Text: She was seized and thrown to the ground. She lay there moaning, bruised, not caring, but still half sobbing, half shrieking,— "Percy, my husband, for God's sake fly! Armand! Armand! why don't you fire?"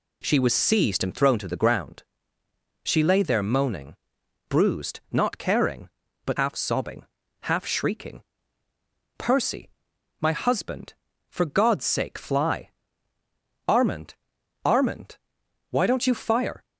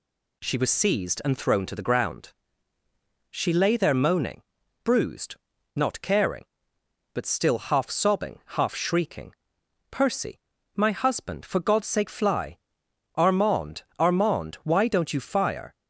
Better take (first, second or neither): second